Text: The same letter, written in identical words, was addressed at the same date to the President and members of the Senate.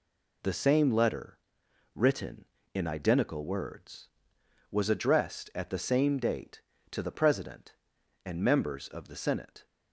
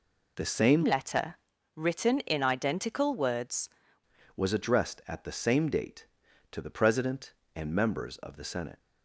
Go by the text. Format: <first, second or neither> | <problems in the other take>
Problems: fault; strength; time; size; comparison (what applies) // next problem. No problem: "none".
first | changes voice from "letter" to "words"; from 0.8 to 3.6 s; 2.8 s long